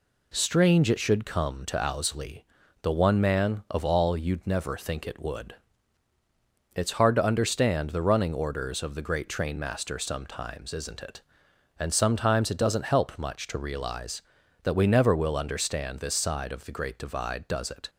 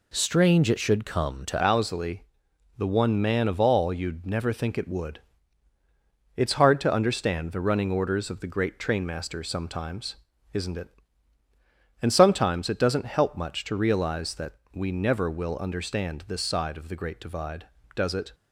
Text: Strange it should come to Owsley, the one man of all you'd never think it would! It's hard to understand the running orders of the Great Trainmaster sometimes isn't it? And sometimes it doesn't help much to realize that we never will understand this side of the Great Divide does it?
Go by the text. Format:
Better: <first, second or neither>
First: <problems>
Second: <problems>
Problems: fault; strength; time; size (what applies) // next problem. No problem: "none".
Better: first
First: none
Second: changes voice at "Owsley"; from 1.6 s on; 16.7 s long // pauses between "sometimes" and "isn't"; at 10.1 s; 0.38 s long // pauses between "that" and "we"; slight; at 14.5 s; 0.18 s long